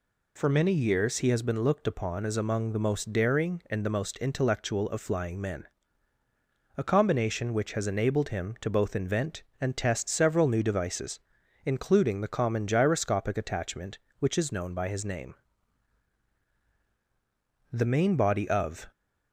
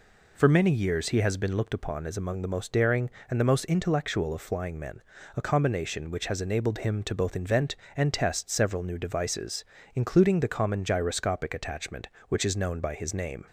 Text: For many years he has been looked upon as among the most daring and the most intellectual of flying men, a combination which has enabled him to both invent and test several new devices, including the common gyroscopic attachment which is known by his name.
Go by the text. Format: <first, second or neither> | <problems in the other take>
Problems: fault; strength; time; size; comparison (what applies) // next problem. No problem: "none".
second | goes on to say "The main body of"; noticeable; from 17.7 s on; 1.2 s long